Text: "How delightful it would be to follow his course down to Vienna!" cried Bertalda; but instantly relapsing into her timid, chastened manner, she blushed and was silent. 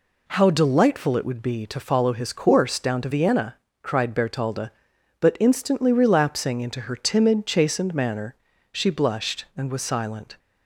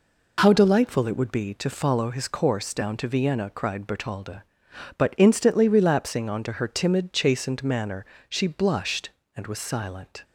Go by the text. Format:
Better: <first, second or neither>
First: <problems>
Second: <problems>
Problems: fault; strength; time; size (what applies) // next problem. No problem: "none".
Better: first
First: none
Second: says "onto" for "into"; at 6.2 s